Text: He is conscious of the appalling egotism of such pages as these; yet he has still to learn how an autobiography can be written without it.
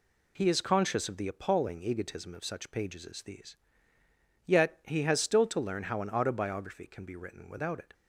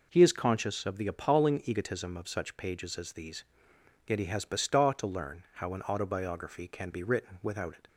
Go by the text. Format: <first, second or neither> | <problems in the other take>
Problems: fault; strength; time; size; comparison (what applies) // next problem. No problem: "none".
first | says "bestaw" for "still"; at 4.4 s